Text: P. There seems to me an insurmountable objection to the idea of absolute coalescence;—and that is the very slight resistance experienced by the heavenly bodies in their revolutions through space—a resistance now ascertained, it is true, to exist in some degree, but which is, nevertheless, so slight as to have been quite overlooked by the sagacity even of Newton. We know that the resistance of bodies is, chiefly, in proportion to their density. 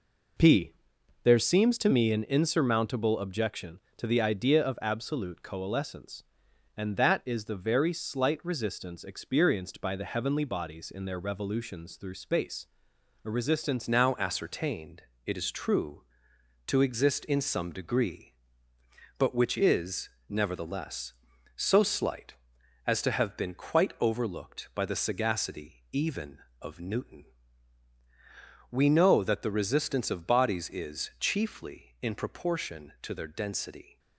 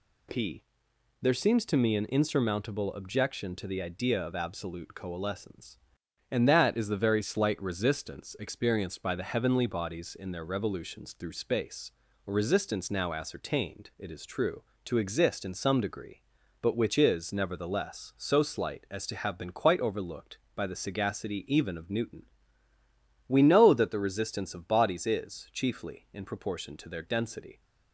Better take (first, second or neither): second